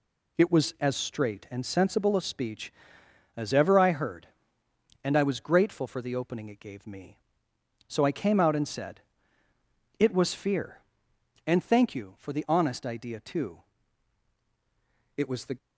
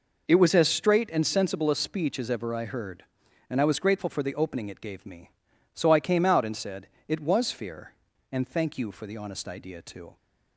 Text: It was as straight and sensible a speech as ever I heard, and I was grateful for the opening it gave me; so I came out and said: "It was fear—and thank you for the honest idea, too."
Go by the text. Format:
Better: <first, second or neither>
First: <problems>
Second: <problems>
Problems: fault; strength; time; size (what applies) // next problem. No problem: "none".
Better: second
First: goes on to say "It was the"; slight; from 15.1 s on; 0.40 s long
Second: none